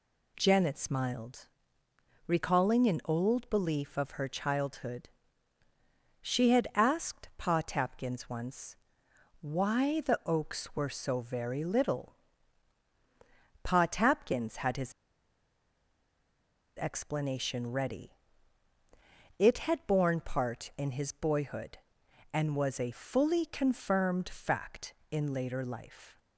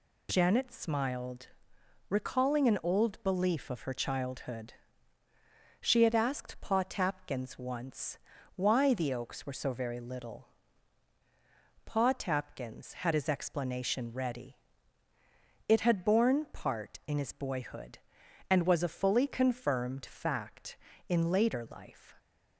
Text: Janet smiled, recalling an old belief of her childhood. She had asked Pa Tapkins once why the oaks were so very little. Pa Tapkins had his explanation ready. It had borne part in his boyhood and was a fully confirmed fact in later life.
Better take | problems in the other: second | pauses between "once" and "why"; noticeable; at 8.7 s; 0.66 s long; also in the second // pauses between "his" and "explanation"; strong; at 14.9 s; 1.8 s long

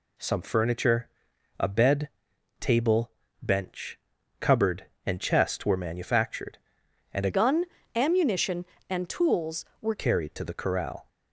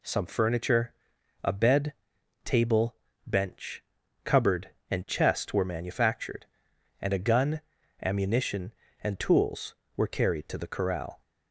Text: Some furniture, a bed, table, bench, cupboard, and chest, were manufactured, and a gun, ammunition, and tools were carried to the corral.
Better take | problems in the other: second | changes voice from "gun" to "were"; from 7.3 to 9.9 s; 2.6 s long

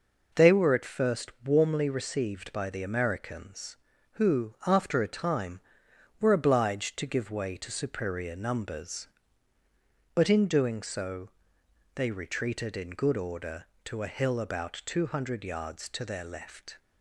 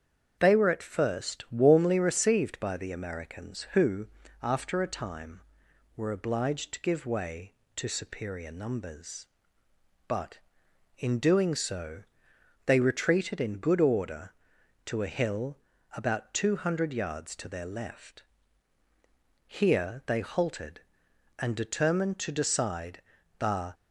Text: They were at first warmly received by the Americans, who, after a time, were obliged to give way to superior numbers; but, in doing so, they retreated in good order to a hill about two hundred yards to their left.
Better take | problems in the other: first | starts louder than the rest; strong; until 1.4 s; 8 dB // pauses between "hill" and "about"; slight; at 15.5 s; 0.36 s long // goes on to say "Here they halted and determined to decide the"; strong; from 19.4 s on; 4.2 s long

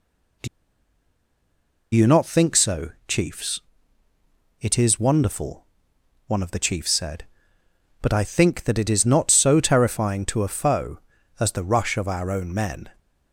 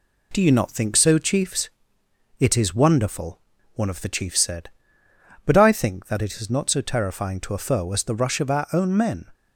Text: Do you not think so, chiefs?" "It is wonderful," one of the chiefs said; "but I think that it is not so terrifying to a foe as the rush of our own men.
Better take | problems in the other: second | pauses between "Do" and "you"; strong; at 0.4 s; 1.4 s long

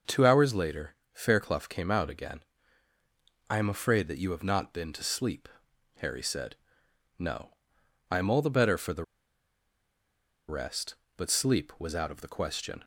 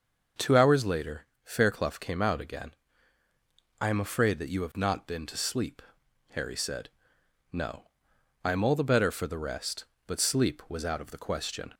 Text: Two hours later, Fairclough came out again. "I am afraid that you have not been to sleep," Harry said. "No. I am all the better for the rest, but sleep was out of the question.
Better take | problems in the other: second | pauses between "the" and "rest"; strong; at 9.0 s; 1.4 s long

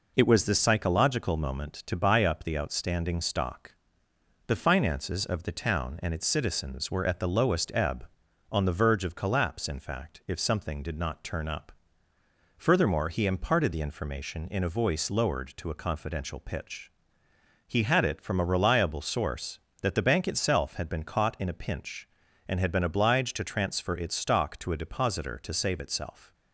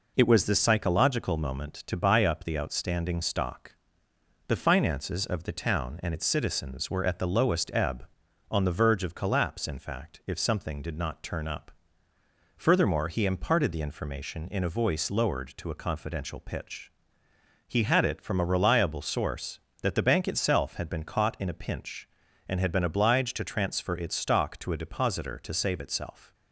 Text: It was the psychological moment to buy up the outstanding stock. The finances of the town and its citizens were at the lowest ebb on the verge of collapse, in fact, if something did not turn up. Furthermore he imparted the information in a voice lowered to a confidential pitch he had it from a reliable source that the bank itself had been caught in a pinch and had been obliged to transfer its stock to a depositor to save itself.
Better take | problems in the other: neither | pauses between "pitch" and "he"; noticeable; the same in both

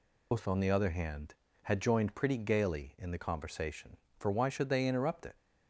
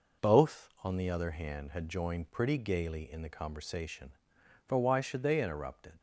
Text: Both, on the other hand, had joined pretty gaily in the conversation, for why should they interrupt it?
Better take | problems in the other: second | loses the start of "Both"; at 0.3 s; 160 ms

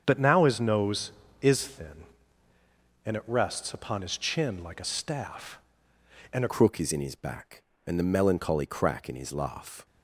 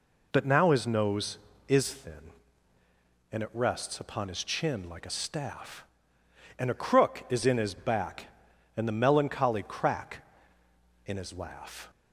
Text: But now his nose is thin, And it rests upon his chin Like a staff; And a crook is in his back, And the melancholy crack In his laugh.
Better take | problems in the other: second | starts louder than the rest; strong; until 1.0 s; 7.5 dB // changes voice at "crook"; from 6.5 s on; 3.3 s long

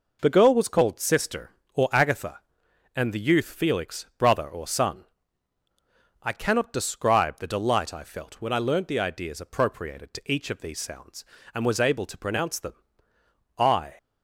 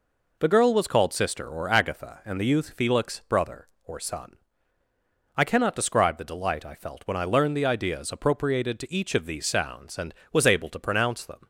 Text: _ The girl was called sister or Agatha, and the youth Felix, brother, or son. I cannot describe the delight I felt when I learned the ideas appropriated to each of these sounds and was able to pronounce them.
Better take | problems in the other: second | goes on to say "I"; slight; from 13.5 s on; 0.38 s long

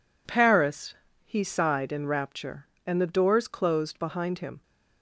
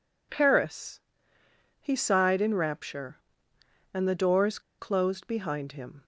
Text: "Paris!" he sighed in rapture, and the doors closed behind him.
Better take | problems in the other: first | pauses between "doors" and "closed"; slight; at 4.5 s; 0.19 s long

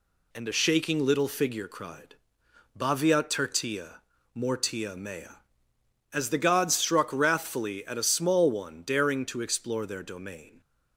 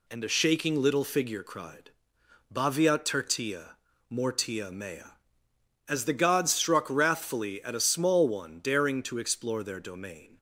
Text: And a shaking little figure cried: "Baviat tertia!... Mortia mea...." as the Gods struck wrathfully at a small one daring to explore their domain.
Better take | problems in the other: neither | none

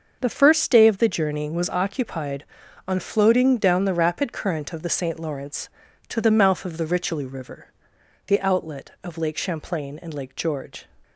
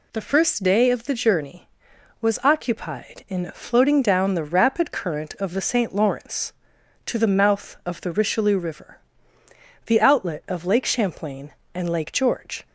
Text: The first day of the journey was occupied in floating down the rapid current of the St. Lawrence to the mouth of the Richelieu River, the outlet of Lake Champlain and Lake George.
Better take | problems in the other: second | starts louder than the rest; until 1.2 s; 6 dB // says "on" for "in"; at 2.8 s

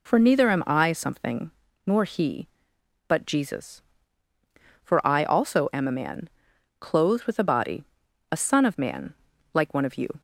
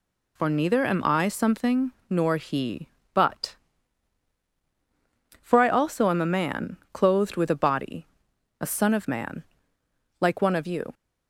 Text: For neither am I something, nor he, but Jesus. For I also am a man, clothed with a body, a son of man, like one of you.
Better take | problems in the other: first | skips "Jesus"; at 4.4 s

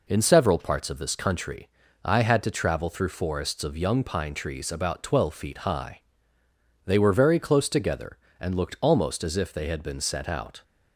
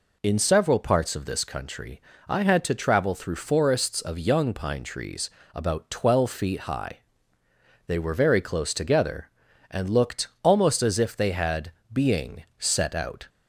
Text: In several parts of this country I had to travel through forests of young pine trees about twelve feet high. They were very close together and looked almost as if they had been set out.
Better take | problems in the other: first | pauses between "country" and "I"; slight; at 2.0 s; 0.28 s long; also in the first // pauses between "trees" and "about"; slight; at 5.3 s; 0.24 s long // pauses between "looked" and "almost"; slight; at 10.2 s; 0.16 s long // says "being" for "been"; at 11.9 s

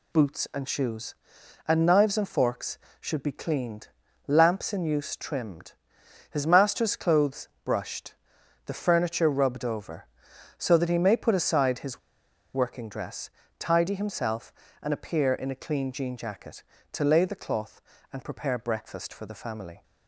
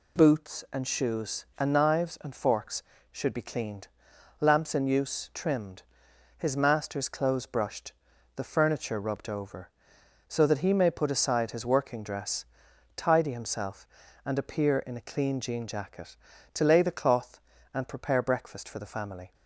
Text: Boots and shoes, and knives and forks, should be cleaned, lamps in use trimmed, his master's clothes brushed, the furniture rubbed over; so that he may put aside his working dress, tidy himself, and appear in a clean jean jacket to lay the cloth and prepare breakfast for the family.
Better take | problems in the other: second | pauses between "clothes" and "brushed"; slight; at 7.4 s; 0.16 s long // pauses between "his" and "working"; noticeable; at 11.9 s; 0.54 s long

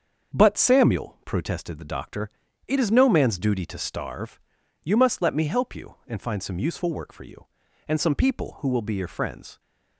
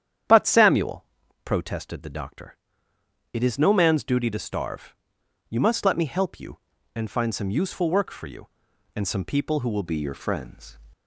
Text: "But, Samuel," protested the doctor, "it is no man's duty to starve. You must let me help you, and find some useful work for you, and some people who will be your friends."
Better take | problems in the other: first | starts louder than the rest; strong; until 1.6 s; 9.5 dB; also in the first // changes voice at "be"; from 9.8 s on; 0.9 s long

